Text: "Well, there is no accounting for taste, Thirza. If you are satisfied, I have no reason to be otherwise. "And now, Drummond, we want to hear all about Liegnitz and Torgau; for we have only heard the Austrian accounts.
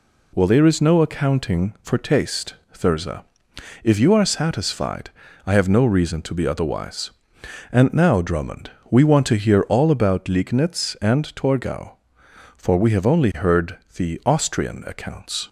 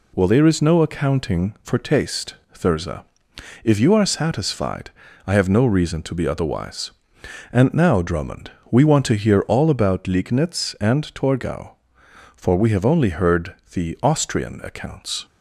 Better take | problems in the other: neither | pauses between "heard" and "the"; slight; the same in both

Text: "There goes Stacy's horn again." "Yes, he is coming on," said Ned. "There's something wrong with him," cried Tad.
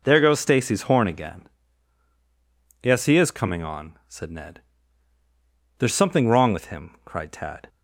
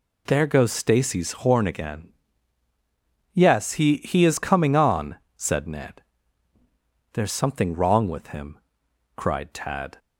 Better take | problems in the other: first | says "he" twice; at 3.9 s

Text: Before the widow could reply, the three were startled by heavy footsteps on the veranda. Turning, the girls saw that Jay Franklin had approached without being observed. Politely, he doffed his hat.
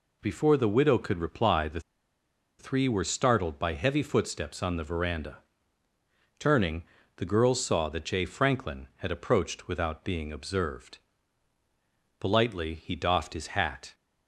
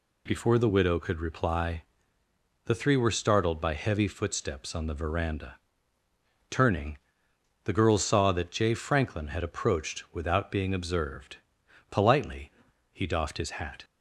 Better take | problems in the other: second | pauses between "the" and "three"; noticeable; at 1.7 s; 0.79 s long

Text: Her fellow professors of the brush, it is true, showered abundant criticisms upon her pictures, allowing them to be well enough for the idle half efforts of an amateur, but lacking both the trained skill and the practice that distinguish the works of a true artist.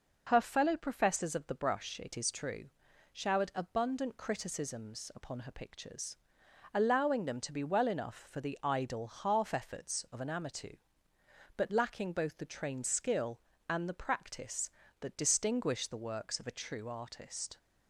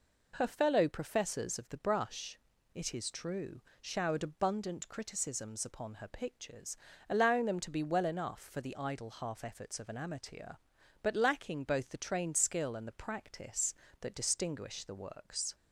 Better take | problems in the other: first | stops before "of a true artist"; at 15.5 s

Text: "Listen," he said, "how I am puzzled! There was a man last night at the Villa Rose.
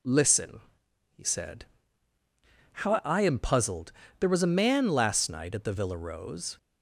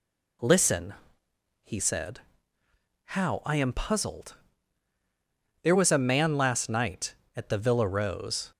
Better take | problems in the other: neither | none

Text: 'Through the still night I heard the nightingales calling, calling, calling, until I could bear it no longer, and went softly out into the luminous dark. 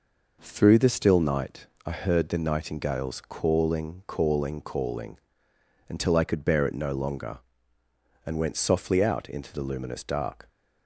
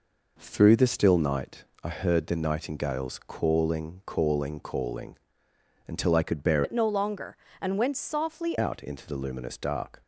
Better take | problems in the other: first | pauses between "night" and "I"; slight; at 1.6 s; 0.20 s long; slight in the first // changes voice from "it" to "softly"; from 6.6 to 8.5 s; 1.9 s long

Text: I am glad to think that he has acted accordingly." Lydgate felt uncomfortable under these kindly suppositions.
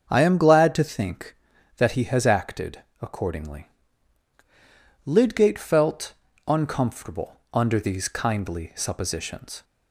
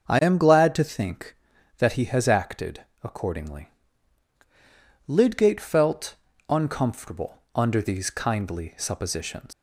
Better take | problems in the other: first | starts louder than the rest; until 1.1 s; 6.5 dB; also in the first // pauses between "acted" and "accordingly"; slight; at 2.8 s; 0.22 s long; slight in the first // pauses between "felt" and "uncomfortable"; slight; at 6.1 s; 0.34 s long; slight in the first // leaves "suppositions" unfinished; at 9.5 s; 125 ms

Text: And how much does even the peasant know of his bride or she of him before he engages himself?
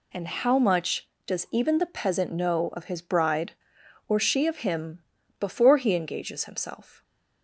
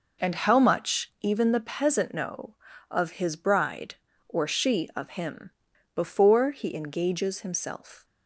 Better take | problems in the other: first | skips "does"; at 1.1 s // pauses between "him" and "before"; at 5.5 s; 0.44 s long; also in the first

